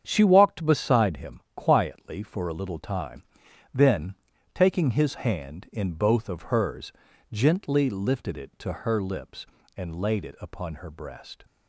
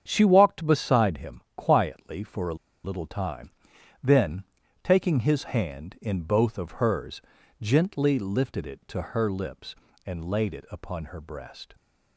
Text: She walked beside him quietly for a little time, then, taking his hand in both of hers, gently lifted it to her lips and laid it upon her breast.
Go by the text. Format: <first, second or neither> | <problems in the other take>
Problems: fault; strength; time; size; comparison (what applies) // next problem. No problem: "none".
first | starts louder than the rest; strong; until 1.0 s; 8 dB; strong in the first // pauses between "him" and "quietly"; slight; at 1.4 s; 0.16 s long; slight in the first // pauses between "a" and "little"; slight; at 2.5 s; 0.29 s long